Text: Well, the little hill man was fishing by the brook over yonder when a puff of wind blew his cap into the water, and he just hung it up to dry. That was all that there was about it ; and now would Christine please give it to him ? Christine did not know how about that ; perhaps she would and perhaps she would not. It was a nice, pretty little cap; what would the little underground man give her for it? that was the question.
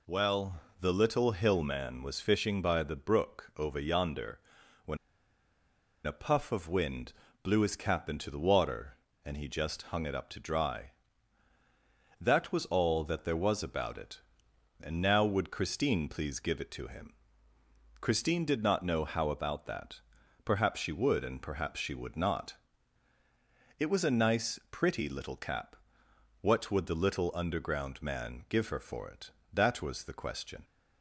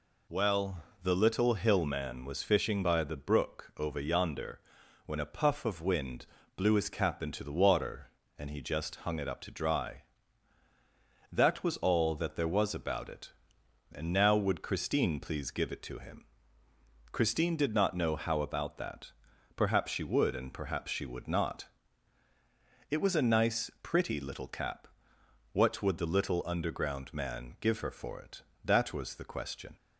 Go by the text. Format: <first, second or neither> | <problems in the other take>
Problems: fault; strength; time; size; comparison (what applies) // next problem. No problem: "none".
second | pauses between "yonder" and "when"; noticeable; at 4.3 s; 0.46 s long; noticeable in the second // pauses between "when" and "a"; at 4.9 s; 1.0 s long // pauses between "wind" and "blew"; slight; at 7.1 s; 0.30 s long; slight in the second